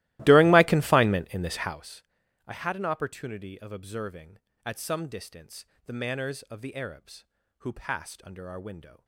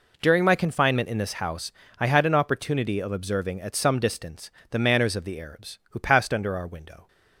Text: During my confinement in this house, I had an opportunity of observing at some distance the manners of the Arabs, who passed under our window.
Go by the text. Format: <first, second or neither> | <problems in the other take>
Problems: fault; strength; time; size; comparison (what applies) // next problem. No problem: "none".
second | starts louder than the rest; strong; until 1.8 s; 17.5 dB // pauses between "distance" and "the"; slight; at 5.6 s; 0.22 s long; slight in the second